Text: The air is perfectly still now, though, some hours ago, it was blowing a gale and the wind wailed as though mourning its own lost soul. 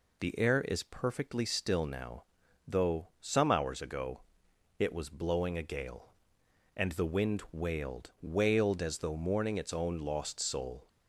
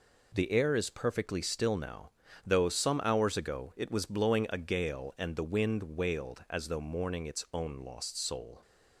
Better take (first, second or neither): second